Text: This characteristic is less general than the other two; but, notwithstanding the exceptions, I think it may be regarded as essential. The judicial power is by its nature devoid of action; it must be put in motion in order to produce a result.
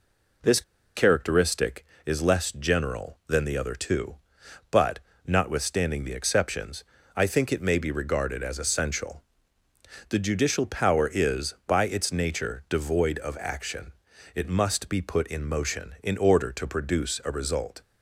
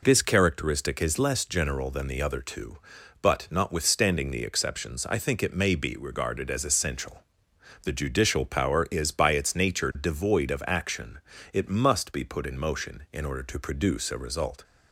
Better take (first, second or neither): second